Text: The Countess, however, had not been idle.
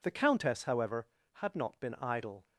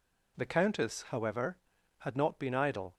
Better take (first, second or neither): neither